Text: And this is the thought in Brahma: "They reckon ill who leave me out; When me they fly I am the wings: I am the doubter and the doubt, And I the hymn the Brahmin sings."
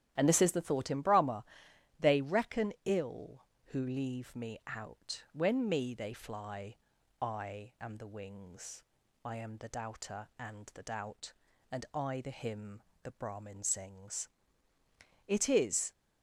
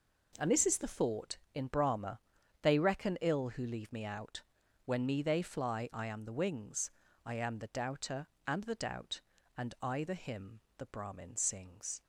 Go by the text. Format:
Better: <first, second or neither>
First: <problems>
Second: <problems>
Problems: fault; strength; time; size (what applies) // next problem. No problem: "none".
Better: second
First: starts louder than the rest; strong; until 1.1 s; 11.5 dB // pauses between "fly" and "I"; at 6.7 s; 0.42 s long // pauses between "hymn" and "the"; slight; at 12.8 s; 0.22 s long // goes on to say "It is"; noticeable; from 15.2 s on; 0.64 s long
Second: pauses between "hymn" and "the"; slight; at 10.5 s; 0.18 s long